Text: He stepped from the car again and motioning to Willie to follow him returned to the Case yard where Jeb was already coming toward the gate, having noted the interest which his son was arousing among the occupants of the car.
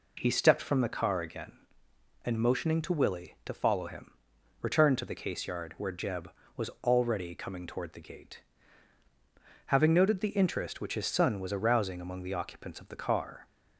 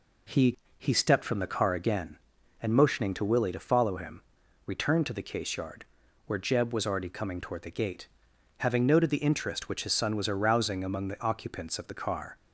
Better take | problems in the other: first | says "He" twice; at 0.7 s // pauses between "him" and "returned"; at 4.2 s; 0.44 s long; noticeable in the first // pauses between "yard" and "where"; at 5.8 s; 0.40 s long

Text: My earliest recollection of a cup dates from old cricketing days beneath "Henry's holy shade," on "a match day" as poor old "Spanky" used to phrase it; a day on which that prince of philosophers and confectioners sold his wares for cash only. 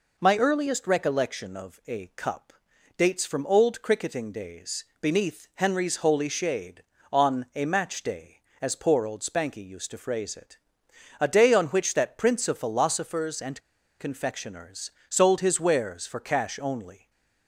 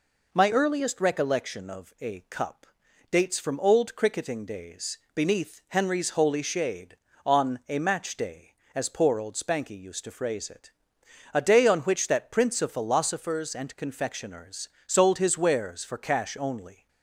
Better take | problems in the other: second | pauses between "cup" and "dates"; noticeable; at 2.5 s; 0.46 s long; noticeable in the second // pauses between "days" and "beneath"; slight; at 4.8 s; 0.16 s long; slight in the second // pauses between "and" and "confectioners"; at 13.6 s; 0.39 s long // pauses between "confectioners" and "sold"; slight; at 14.9 s; 0.18 s long; slight in the second // stays silent after the last word; slight; from 16.9 s on; 0.5 s long

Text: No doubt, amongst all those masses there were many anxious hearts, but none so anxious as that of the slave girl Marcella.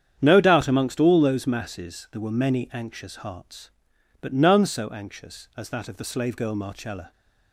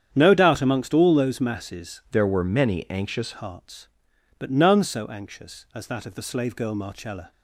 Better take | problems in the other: first | starts louder than the rest; strong; until 1.1 s; 9 dB; strong in the first // changes voice from "there" to "anxious"; from 2.1 to 3.3 s; 1.2 s long

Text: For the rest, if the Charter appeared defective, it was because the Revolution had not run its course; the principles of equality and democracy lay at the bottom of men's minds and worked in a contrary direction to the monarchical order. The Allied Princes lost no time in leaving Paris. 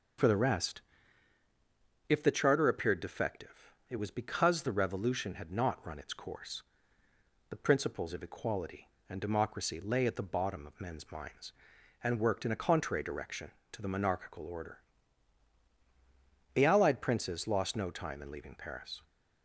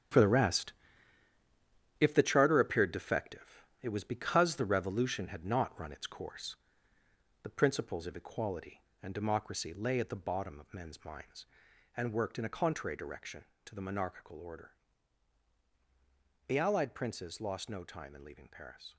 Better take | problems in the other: first | gets quieter; strong; throughout; 10 dB

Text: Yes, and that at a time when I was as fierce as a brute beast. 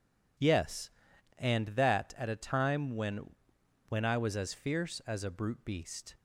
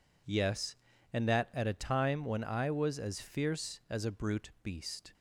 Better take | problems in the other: second | says "when" twice; at 3.8 s

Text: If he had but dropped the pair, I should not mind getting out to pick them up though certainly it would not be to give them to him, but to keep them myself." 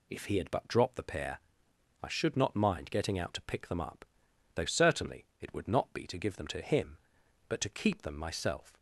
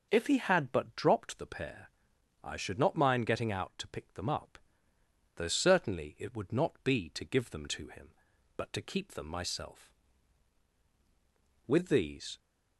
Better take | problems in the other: first | pauses between "up" and "though"; noticeable; at 4.5 s; 0.80 s long; noticeable in the first // goes on to say "With these"; noticeable; from 11.6 s on; 0.70 s long

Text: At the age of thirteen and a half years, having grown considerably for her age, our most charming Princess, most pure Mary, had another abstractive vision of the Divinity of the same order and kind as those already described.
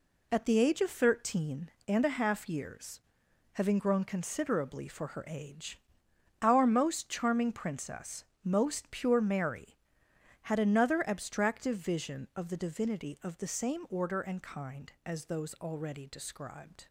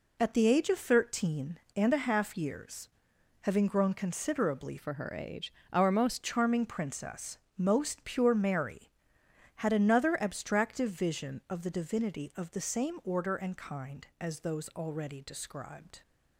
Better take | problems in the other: first | changes voice from "for" to "most"; from 4.7 to 6.2 s; 1.5 s long

